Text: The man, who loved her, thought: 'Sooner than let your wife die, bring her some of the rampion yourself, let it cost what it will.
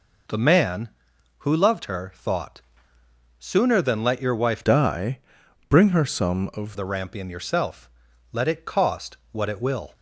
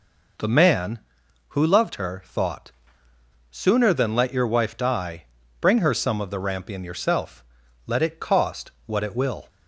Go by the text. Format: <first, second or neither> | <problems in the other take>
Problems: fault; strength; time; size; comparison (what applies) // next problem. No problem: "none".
second | changes voice from "die" to "of"; from 4.6 to 6.7 s; 2.1 s long